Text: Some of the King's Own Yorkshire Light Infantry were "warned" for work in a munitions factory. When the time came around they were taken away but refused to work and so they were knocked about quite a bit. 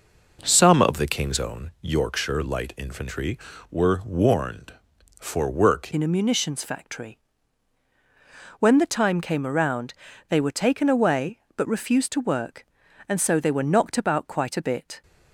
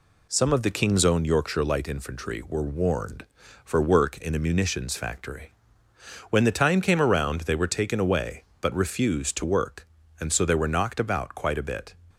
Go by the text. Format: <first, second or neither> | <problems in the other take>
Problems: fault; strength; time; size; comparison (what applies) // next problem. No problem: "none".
second | changes voice at "in"; from 5.9 s on; 9.1 s long // pauses between "around" and "they"; slight; at 9.9 s; 0.36 s long